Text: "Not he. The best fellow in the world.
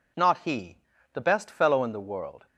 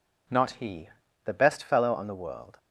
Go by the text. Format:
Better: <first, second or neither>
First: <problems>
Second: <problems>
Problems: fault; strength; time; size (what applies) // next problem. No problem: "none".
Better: first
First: none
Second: says "on" for "in"; at 1.9 s